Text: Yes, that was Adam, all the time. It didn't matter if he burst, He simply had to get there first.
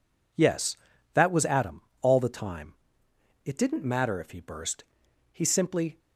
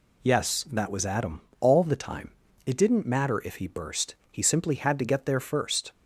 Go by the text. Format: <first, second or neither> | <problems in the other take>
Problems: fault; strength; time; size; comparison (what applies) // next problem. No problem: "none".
second | stops before "had to get there first"; at 5.9 s